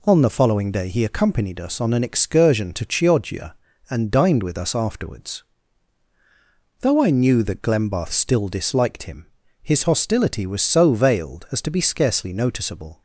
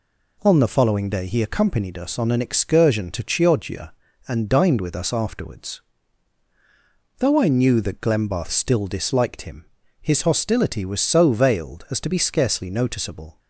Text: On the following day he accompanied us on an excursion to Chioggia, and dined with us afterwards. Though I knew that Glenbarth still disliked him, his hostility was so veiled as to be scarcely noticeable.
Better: neither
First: none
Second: none

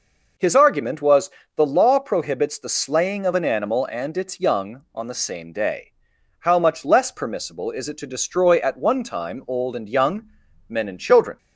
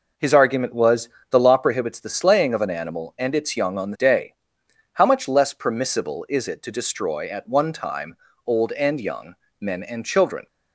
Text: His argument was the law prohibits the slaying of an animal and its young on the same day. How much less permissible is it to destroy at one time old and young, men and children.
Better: first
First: pauses between "was" and "the"; slight; at 1.3 s; 0.24 s long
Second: pauses between "was" and "the"; slight; at 1.0 s; 0.20 s long // skips "same"; at 3.9 s // pauses between "time" and "old"; slight; at 8.1 s; 0.30 s long

